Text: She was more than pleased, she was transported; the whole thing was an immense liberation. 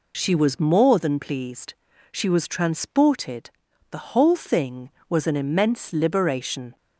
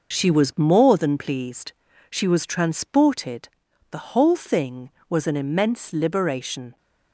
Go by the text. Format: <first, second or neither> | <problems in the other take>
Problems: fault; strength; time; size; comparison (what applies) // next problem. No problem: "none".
first | gets quieter; throughout; 6.5 dB